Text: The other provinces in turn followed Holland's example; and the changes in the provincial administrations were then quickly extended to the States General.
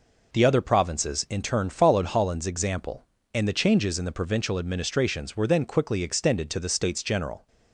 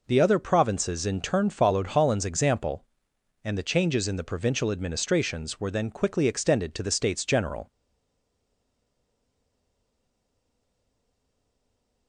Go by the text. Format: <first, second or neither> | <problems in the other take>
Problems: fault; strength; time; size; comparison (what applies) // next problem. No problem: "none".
first | stays silent after the last word; strong; from 7.6 s on; 4.4 s long